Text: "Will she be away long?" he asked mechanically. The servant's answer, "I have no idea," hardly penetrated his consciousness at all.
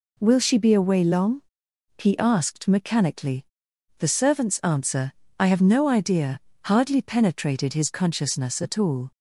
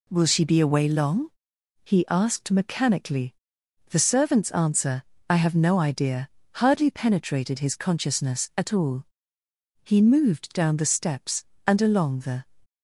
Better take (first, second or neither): first